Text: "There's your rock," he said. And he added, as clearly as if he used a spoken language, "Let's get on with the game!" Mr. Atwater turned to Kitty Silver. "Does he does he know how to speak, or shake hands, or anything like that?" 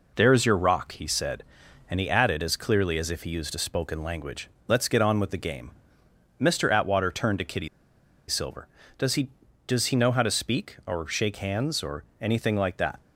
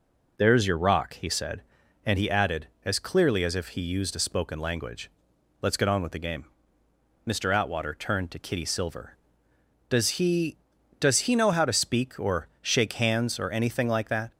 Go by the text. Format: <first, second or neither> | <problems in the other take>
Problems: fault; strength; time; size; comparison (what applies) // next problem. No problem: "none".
second | pauses between "Kitty" and "Silver"; noticeable; at 7.6 s; 0.60 s long // pauses between "or" and "anything"; slight; at 12.0 s; 0.16 s long